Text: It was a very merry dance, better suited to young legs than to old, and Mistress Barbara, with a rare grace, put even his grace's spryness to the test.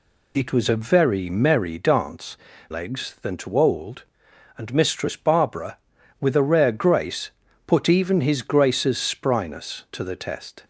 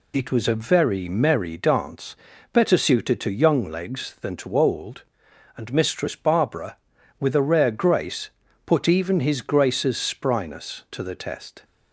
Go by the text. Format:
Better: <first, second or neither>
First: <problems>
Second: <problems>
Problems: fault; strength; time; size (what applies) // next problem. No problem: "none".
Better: second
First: skips "better suited to young"; at 2.5 s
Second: none